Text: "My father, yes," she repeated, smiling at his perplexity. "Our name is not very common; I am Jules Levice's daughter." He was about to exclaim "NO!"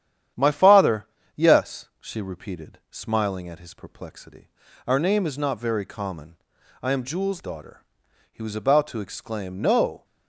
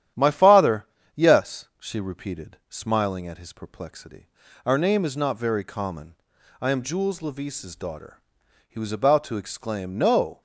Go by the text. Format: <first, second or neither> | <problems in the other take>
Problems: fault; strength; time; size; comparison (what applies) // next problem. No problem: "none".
second | starts louder than the rest; strong; until 1.6 s; 10 dB; strong in the second // skips "Levice's"; at 7.4 s